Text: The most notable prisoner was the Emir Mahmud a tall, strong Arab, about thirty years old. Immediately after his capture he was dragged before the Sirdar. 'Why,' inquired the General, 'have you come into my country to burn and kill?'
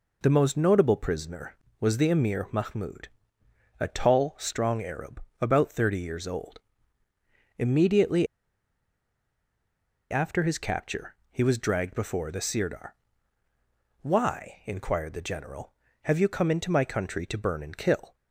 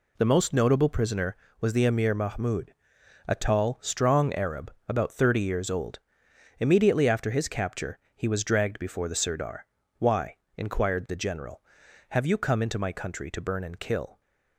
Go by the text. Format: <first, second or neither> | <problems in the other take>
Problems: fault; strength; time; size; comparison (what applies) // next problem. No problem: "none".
second | pauses between "Mahmud" and "a"; noticeable; at 3.0 s; 0.72 s long; noticeable in the second // pauses between "Immediately" and "after"; strong; at 8.2 s; 1.8 s long // pauses between "capture" and "he"; slight; at 11.1 s; 0.16 s long; slight in the second